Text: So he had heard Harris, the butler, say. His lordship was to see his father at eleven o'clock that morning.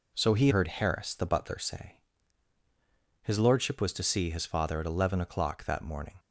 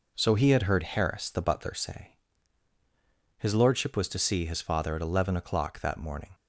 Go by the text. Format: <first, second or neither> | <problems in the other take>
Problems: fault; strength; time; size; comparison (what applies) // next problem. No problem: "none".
second | skips "had"; at 0.4 s